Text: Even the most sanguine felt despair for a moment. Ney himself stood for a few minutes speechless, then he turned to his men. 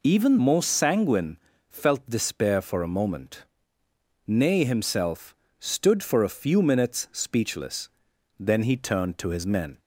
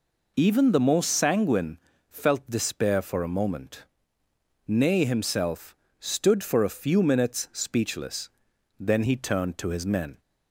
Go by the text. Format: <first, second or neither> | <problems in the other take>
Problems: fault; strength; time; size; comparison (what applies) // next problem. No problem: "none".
second | skips "the"; at 0.3 s // pauses between "sanguine" and "felt"; slight; at 1.3 s; 0.30 s long; slight in the second // pauses between "himself" and "stood"; slight; at 5.3 s; 0.24 s long; slight in the second